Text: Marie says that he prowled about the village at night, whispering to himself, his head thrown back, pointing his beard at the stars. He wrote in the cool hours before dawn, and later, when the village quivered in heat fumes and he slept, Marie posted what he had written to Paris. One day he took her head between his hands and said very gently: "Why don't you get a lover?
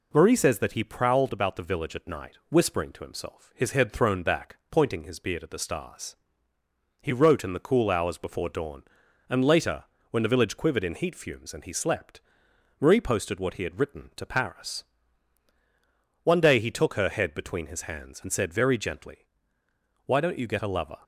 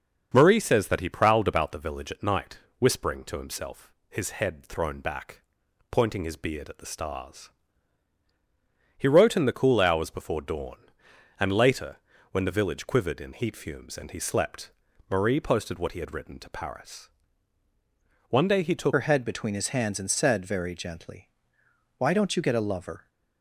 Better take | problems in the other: first | starts louder than the rest; until 1.3 s; 6.5 dB // changes voice at "her"; from 18.9 s on; 4.1 s long

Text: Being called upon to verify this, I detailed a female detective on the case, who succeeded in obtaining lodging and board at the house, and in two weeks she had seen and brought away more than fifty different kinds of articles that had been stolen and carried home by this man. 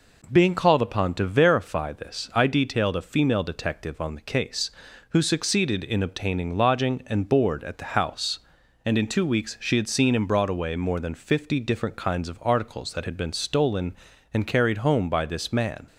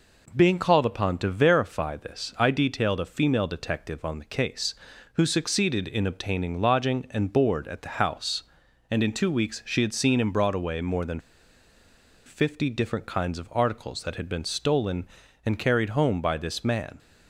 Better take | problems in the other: first | pauses between "than" and "fifty"; at 11.1 s; 1.0 s long

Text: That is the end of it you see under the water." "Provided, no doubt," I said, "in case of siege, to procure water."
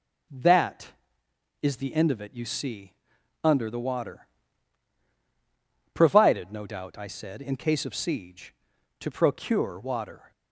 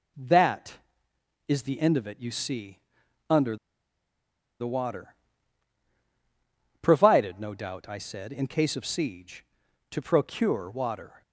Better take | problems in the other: first | starts louder than the rest; until 1.9 s; 6 dB // pauses between "see" and "under"; noticeable; at 2.7 s; 0.50 s long; noticeable in the first // pauses between "under" and "the"; at 3.5 s; 1.0 s long

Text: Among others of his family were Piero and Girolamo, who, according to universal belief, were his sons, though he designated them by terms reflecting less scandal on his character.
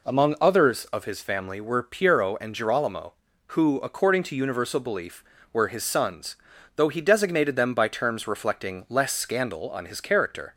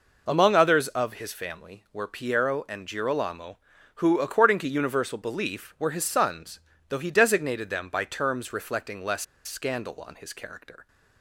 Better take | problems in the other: first | pauses between "less" and "scandal"; slight; at 9.2 s; 0.22 s long

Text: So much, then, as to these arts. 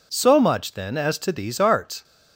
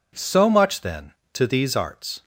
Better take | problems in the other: first | skips "as"; at 1.2 s

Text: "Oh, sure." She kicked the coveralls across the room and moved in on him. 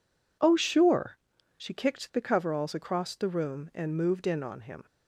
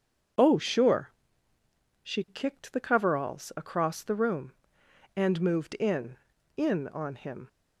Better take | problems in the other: first | starts louder than the rest; strong; until 2.3 s; 7 dB // says "in" twice; at 6.5 s

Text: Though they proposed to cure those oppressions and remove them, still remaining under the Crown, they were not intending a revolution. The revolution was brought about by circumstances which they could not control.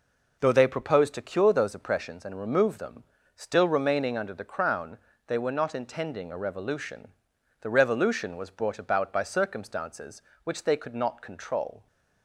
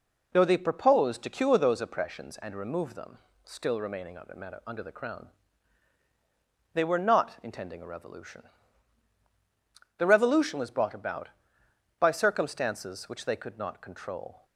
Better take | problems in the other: first | says "under" twice; at 4.6 s

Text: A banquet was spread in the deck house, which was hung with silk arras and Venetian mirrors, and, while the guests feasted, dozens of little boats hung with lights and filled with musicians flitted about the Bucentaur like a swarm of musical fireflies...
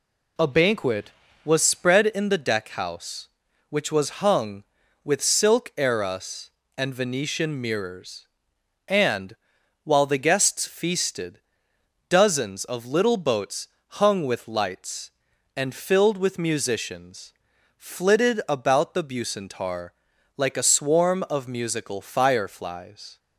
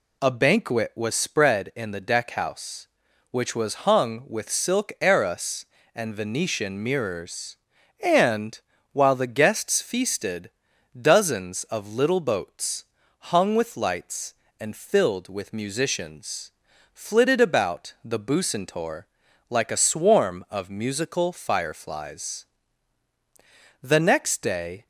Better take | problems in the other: first | pauses between "boats" and "hung"; slight; at 12.8 s; 0.34 s long; slight in the first // pauses between "musicians" and "flitted"; at 16.5 s; 0.44 s long; noticeable in the first // pauses between "Bucentaur" and "like"; noticeable; at 19.0 s; 0.46 s long; also in the first // goes on to say "The next day"; noticeable; from 23.8 s on; 1.0 s long

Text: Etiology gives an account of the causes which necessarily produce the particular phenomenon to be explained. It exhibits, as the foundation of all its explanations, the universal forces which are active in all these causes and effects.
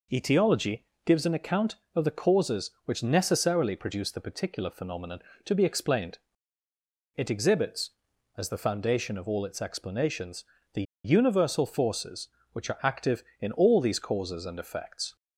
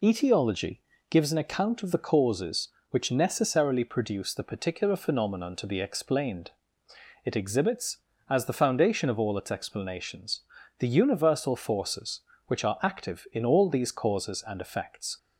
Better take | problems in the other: second | pauses between "Etiology" and "gives"; slight; at 0.8 s; 0.20 s long; slight in the second // pauses between "the" and "universal"; slight; at 10.8 s; 0.22 s long

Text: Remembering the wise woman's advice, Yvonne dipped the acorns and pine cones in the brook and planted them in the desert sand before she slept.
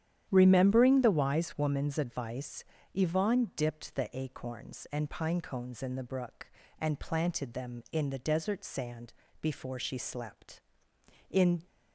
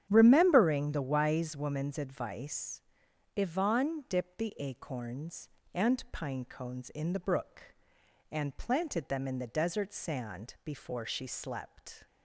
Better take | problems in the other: second | starts louder than the rest; strong; until 1.3 s; 10.5 dB; strong in the second // pauses between "sand" and "before"; slight; at 9.1 s; 0.30 s long // goes on to say "In"; slight; from 11.2 s on; 0.36 s long

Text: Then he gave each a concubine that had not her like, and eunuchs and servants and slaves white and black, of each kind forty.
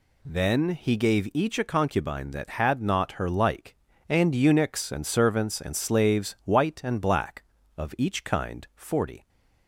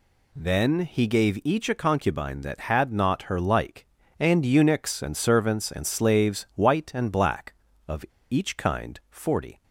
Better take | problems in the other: first | pauses between "of" and "each"; slight; at 8.0 s; 0.26 s long

